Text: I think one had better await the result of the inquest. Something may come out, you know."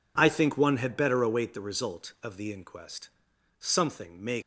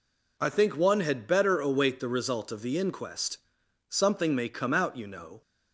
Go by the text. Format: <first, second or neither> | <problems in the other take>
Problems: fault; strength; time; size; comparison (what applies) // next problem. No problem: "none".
second | stops before "come out you know"; at 4.4 s